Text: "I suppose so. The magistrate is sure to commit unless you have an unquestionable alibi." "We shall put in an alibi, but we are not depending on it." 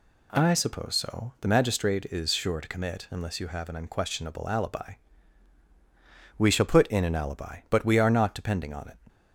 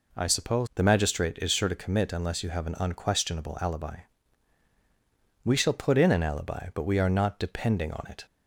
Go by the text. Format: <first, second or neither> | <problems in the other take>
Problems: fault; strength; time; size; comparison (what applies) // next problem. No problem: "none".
first | skips "so"; at 0.7 s